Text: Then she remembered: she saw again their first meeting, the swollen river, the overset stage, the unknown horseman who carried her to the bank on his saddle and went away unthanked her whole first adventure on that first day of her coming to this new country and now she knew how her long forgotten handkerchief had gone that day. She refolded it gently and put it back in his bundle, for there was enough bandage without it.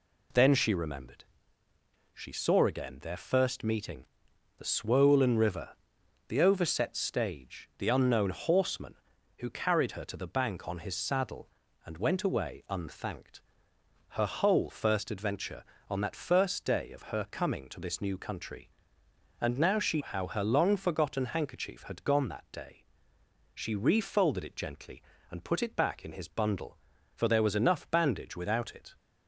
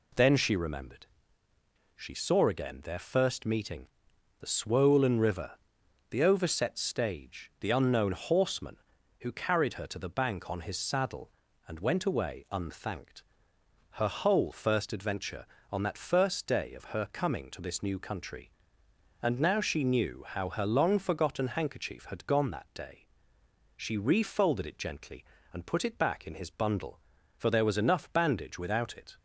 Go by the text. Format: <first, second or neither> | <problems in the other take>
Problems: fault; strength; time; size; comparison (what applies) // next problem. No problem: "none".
second | pauses between "unthanked" and "her"; noticeable; at 13.4 s; 0.74 s long; noticeable in the second // skips "knew"; at 20.0 s